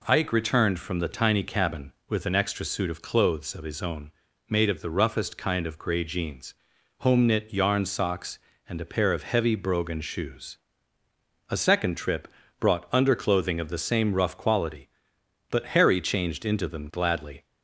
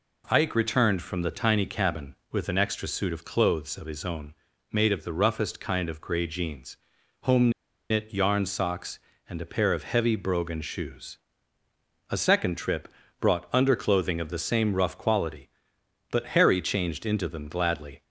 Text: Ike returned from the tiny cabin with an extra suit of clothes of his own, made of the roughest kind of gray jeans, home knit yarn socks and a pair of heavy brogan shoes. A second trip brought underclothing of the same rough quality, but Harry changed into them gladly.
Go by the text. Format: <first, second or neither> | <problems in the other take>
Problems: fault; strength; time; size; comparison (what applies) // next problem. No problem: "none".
first | pauses between "home" and "knit"; at 7.5 s; 0.39 s long // pauses between "trip" and "brought"; slight; at 12.8 s; 0.32 s long; slight in the first